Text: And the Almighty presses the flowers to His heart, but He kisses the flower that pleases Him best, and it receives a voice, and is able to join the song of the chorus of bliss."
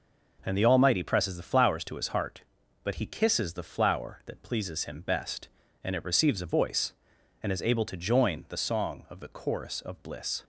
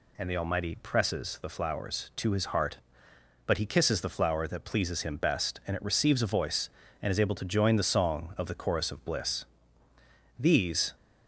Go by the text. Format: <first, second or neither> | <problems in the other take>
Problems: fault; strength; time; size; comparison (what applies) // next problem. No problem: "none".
first | goes on to say "These"; from 10.3 s on; 0.56 s long